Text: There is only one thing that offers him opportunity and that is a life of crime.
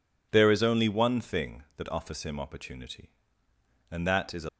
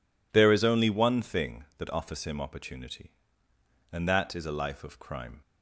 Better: second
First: stops before "life of crime"; at 4.4 s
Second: none

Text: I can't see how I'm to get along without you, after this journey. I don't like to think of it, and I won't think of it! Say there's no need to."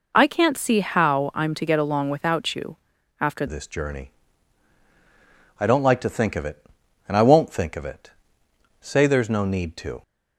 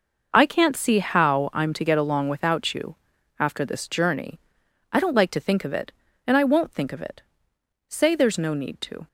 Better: second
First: changes voice at "this"; from 3.4 s on; 6.6 s long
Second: none

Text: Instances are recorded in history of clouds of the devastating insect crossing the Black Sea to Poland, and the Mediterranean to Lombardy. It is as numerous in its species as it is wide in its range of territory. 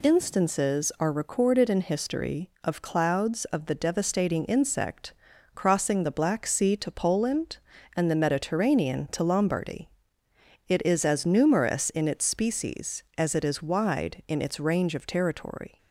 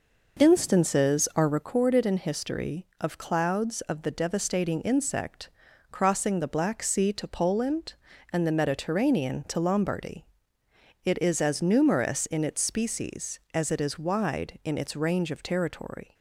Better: first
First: pauses between "insect" and "crossing"; at 5.1 s; 0.40 s long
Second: starts louder than the rest; noticeable; until 1.7 s; 5.5 dB // pauses between "insect" and "crossing"; at 5.4 s; 0.40 s long

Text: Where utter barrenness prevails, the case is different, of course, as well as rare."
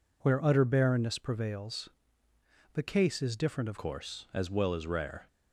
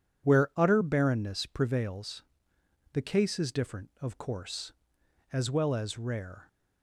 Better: second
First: changes voice at "course"; from 3.7 s on; 1.5 s long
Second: none

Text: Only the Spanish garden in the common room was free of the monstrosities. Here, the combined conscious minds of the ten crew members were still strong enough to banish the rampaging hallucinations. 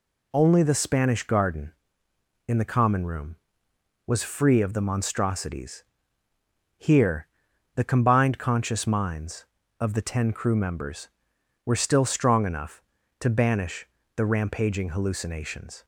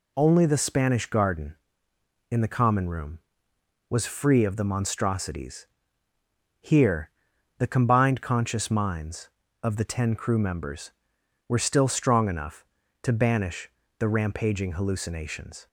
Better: neither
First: pauses between "banish" and "the"; slight; at 13.8 s; 0.30 s long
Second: pauses between "banish" and "the"; slight; at 13.6 s; 0.30 s long

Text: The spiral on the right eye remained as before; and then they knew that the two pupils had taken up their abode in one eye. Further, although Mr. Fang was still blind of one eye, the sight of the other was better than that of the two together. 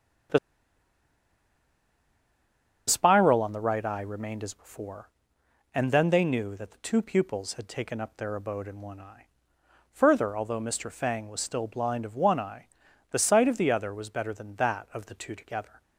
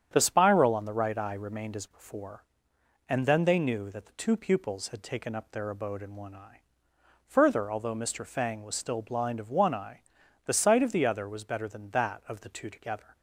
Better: second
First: starts louder than the rest; strong; until 3.8 s; 8.5 dB // pauses between "The" and "spiral"; strong; at 0.3 s; 2.4 s long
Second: starts louder than the rest; strong; until 1.1 s; 9 dB

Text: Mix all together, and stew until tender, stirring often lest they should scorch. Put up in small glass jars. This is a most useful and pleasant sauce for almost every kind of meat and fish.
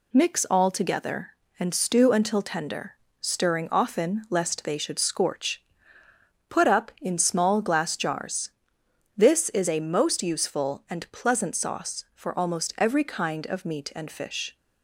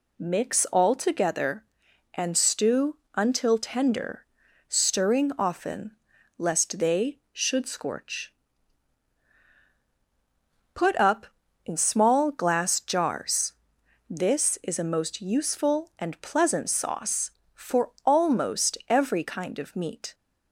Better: first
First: none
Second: pauses between "stew" and "until"; slight; at 2.9 s; 0.18 s long // pauses between "often" and "lest"; noticeable; at 5.9 s; 0.46 s long // stops before "and fish"; at 20.1 s

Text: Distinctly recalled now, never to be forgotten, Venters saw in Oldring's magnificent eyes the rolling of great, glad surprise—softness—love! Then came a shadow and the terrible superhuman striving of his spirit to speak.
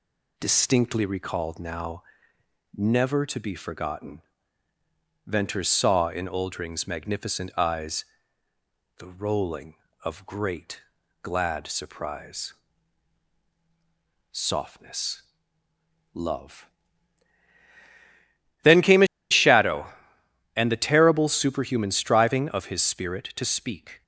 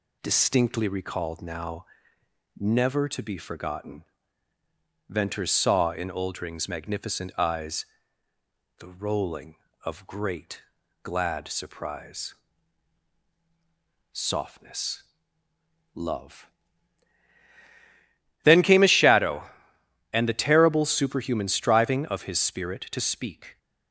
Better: second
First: pauses between "eyes" and "the"; noticeable; at 8.0 s; 0.94 s long // pauses between "a" and "shadow"; slight; at 19.0 s; 0.24 s long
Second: pauses between "eyes" and "the"; noticeable; at 7.8 s; 0.94 s long

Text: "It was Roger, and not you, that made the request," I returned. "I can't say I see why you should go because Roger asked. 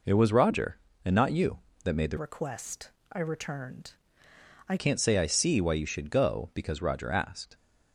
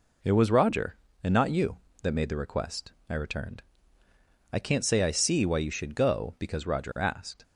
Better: second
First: changes voice from "request" to "I"; from 2.1 to 4.7 s; 2.6 s long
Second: none

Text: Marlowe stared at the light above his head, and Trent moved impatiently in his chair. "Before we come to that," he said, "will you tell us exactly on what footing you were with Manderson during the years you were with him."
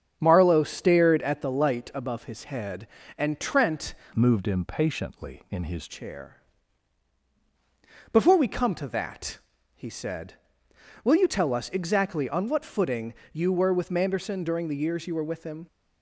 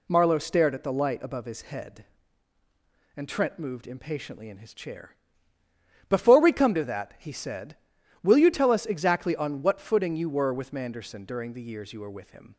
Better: second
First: starts louder than the rest; strong; until 1.2 s; 7.5 dB // changes voice from "moved" to "his"; from 4.1 to 5.8 s; 1.7 s long // pauses between "footing" and "you"; slight; at 13.1 s; 0.20 s long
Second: none

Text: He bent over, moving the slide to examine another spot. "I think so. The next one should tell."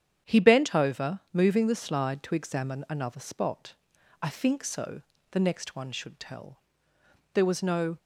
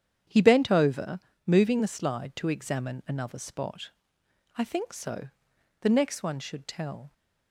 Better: second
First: starts louder than the rest; strong; until 1.4 s; 9 dB // goes on to say "There was no"; noticeable; from 7.3 s on; 0.64 s long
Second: starts louder than the rest; strong; until 1.5 s; 9 dB

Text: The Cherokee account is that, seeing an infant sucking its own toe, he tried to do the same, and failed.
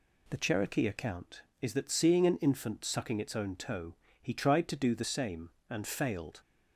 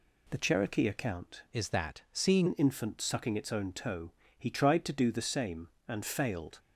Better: first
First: none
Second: changes voice from "is" to "seeing"; from 1.5 to 2.4 s; 0.9 s long

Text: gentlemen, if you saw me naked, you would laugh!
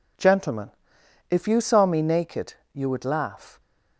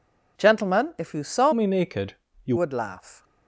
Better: first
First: none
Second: changes voice from "me" to "you"; from 1.5 to 2.5 s; 1.0 s long

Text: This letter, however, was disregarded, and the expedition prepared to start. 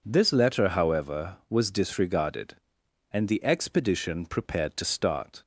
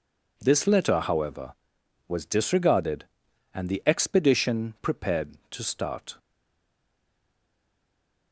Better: first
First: none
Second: stays silent after the last word; from 6.1 s on; 2.2 s long

